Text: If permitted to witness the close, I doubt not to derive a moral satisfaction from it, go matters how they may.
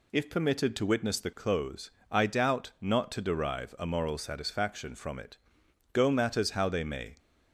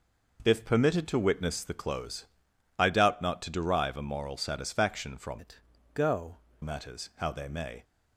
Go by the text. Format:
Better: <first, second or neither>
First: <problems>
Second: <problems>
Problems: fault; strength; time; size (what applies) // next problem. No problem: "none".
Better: first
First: none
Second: changes voice from "it" to "go"; from 5.3 to 6.3 s; 1.0 s long